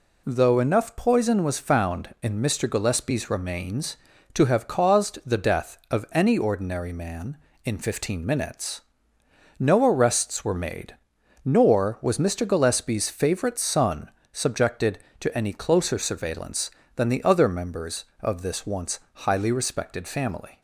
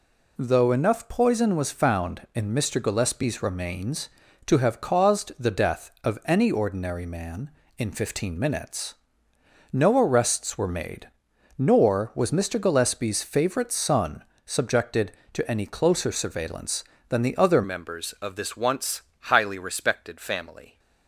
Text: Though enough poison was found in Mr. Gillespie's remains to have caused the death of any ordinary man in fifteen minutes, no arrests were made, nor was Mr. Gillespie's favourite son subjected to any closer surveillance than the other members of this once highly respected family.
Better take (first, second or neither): first